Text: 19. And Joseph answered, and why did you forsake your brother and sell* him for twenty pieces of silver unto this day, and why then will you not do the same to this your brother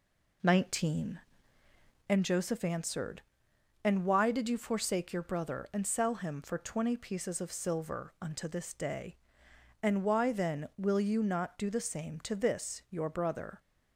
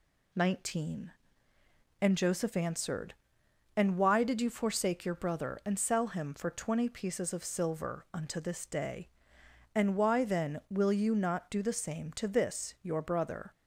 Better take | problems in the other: second | starts louder than the rest; until 2.1 s; 3.5 dB

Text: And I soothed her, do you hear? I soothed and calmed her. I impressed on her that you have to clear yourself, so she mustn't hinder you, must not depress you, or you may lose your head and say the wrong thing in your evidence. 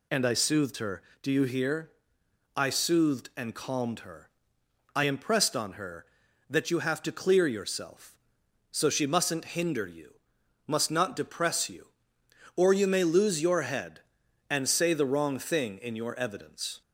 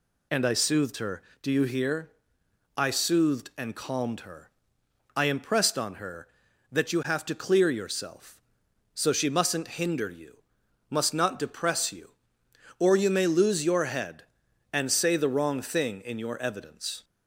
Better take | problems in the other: neither | none

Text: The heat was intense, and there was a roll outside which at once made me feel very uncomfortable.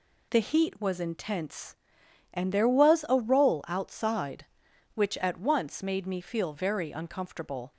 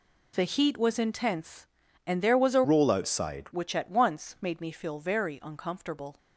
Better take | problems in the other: first | changes voice from "roll" to "outside"; from 2.6 to 3.4 s; 0.8 s long

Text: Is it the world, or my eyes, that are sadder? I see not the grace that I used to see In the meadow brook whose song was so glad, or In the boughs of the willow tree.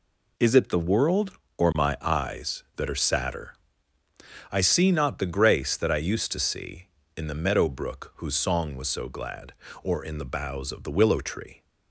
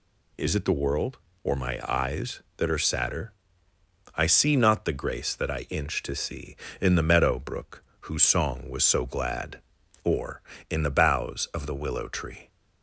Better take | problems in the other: first | says "inch" for "used"; at 5.6 s // pauses between "brook" and "whose"; slight; at 7.8 s; 0.18 s long

